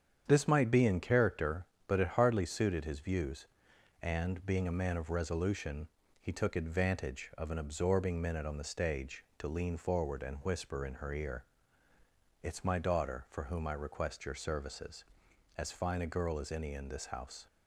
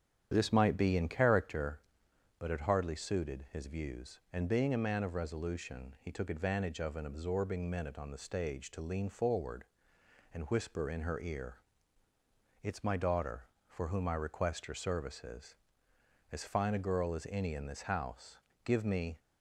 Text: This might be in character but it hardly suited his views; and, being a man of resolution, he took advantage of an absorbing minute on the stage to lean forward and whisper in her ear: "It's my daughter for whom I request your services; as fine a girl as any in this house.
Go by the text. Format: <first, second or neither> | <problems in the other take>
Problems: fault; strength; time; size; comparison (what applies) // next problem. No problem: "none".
first | starts louder than the rest; strong; until 1.3 s; 9.5 dB; strong in the first // goes on to say "Give me"; from 18.6 s on; 0.54 s long